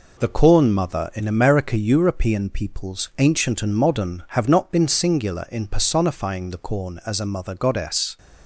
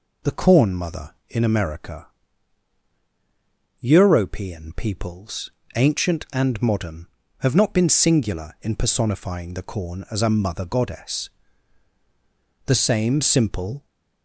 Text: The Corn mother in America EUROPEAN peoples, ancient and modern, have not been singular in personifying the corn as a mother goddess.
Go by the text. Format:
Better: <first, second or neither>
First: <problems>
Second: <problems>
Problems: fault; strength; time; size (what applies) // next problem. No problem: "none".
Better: first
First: none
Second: pauses between "America" and "EUROPEAN"; strong; at 2.0 s; 1.7 s long // goes on to say "The same simple"; noticeable; from 12.6 s on; 1.2 s long